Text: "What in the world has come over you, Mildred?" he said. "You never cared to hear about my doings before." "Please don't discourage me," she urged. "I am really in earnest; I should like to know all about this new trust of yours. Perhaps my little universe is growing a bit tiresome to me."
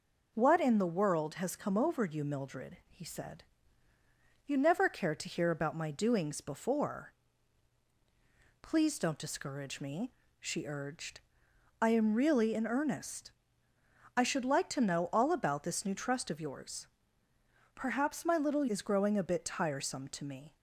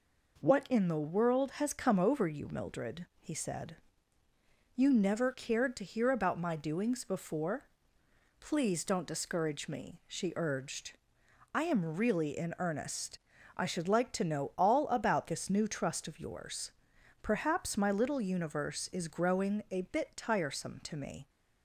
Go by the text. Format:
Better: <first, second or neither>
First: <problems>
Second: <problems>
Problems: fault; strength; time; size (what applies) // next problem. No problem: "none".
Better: second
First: skips "universe"; at 18.6 s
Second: none